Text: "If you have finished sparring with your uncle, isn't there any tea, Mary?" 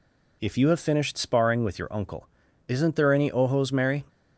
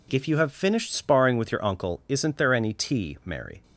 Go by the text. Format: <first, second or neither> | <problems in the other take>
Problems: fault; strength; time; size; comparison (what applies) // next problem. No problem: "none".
second | says "ojos" for "tea"; at 3.2 s